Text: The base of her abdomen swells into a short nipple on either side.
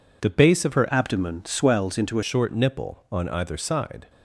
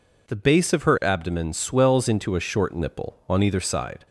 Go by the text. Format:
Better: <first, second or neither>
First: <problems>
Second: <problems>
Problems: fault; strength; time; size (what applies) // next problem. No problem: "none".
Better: second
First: changes voice from "abdomen" to "a"; from 0.8 to 2.2 s; 1.4 s long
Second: none